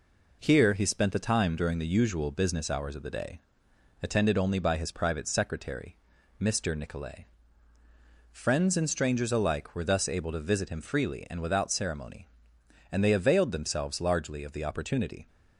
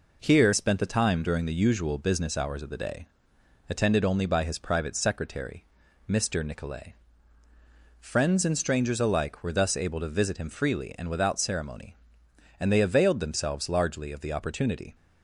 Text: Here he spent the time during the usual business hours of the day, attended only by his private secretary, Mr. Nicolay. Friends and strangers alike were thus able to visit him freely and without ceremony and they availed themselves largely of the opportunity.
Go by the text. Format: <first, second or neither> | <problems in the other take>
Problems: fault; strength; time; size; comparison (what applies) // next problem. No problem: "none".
first | skips "he"; at 0.5 s